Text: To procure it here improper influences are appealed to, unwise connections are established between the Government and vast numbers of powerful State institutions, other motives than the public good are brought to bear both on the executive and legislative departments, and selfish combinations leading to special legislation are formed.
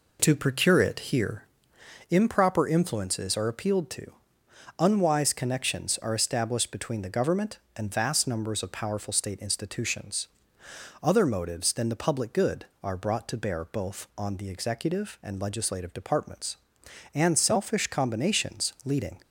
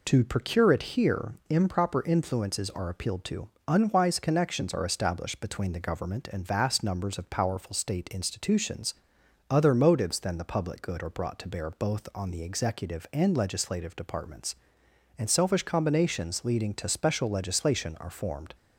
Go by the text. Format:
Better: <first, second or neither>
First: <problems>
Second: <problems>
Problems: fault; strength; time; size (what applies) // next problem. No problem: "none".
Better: second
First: pauses between "here" and "improper"; noticeable; at 1.4 s; 0.66 s long // stops before "to special legislation are formed"; at 19.2 s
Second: pauses between "here" and "improper"; slight; at 1.3 s; 0.16 s long